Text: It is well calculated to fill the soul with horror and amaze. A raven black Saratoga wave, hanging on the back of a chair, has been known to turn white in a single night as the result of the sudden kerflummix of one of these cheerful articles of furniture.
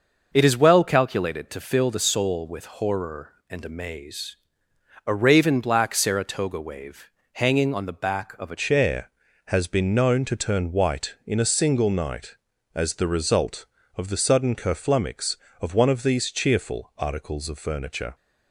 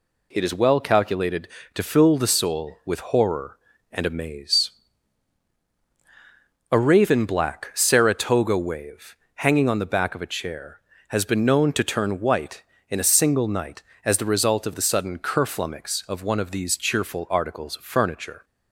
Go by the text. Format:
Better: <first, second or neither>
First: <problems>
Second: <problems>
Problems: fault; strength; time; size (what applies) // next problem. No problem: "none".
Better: second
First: starts louder than the rest; noticeable; until 1.3 s; 6 dB // changes voice at "chair"; from 8.5 s on; 9.6 s long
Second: none